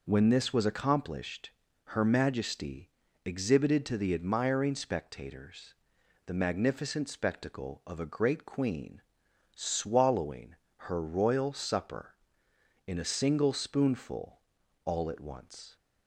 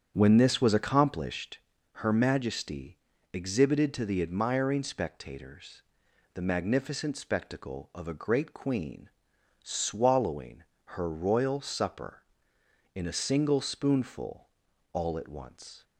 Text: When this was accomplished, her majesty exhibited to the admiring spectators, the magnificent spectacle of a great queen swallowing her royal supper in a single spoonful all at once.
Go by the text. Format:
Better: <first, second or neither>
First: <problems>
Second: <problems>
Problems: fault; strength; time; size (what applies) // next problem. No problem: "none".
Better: first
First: pauses between "majesty" and "exhibited"; at 2.8 s; 0.38 s long // pauses between "queen" and "swallowing"; noticeable; at 9.0 s; 0.52 s long // pauses between "swallowing" and "her"; slight; at 10.5 s; 0.32 s long // pauses between "spoonful" and "all"; noticeable; at 14.3 s; 0.46 s long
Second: starts louder than the rest; strong; until 1.6 s; 8 dB // pauses between "majesty" and "exhibited"; at 2.9 s; 0.38 s long // pauses between "queen" and "swallowing"; noticeable; at 9.0 s; 0.52 s long // pauses between "swallowing" and "her"; slight; at 10.6 s; 0.32 s long // pauses between "spoonful" and "all"; noticeable; at 14.4 s; 0.46 s long